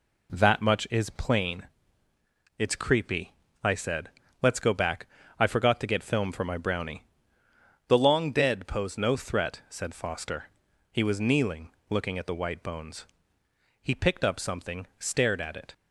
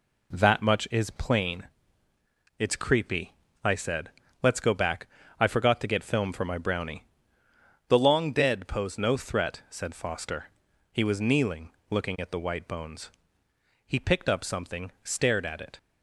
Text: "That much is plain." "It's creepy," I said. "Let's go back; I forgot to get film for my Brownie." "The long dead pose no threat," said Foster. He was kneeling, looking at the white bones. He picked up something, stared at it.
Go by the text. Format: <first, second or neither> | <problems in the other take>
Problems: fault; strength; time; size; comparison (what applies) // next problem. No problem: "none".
neither | none